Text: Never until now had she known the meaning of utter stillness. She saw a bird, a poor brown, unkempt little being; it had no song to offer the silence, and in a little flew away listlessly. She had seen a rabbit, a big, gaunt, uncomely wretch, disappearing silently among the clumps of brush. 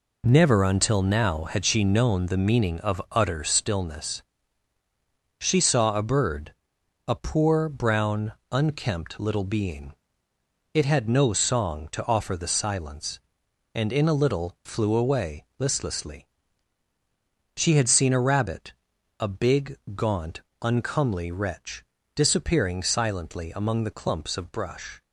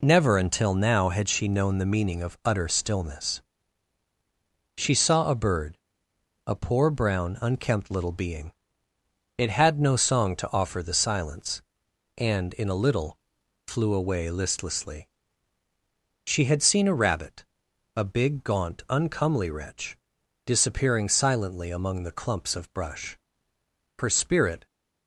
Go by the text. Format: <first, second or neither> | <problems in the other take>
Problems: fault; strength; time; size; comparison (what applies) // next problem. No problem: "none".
first | pauses between "little" and "flew"; noticeable; at 13.1 s; 0.52 s long // goes on to say "Her spirit"; noticeable; from 23.9 s on; 0.66 s long